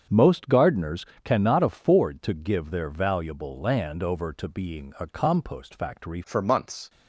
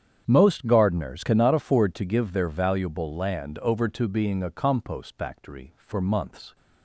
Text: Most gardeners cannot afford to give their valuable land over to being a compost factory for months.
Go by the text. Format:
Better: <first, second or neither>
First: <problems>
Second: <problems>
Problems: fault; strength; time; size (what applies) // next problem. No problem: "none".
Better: second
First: starts louder than the rest; strong; until 1.3 s; 7 dB // pauses between "gardeners" and "cannot"; slight; at 1.0 s; 0.20 s long // changes voice at "for"; from 6.2 s on; 0.6 s long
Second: starts louder than the rest; strong; until 1.2 s; 8.5 dB